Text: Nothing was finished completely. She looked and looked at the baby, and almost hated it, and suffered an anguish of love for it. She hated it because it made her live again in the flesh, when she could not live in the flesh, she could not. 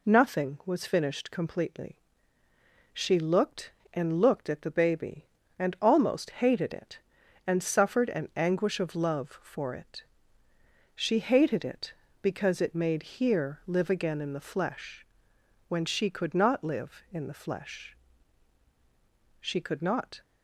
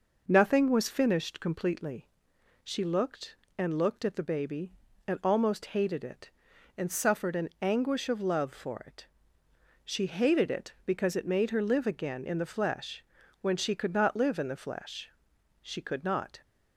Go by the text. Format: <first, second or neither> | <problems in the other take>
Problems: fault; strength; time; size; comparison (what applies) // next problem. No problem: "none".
second | says "here" for "her"; at 13.0 s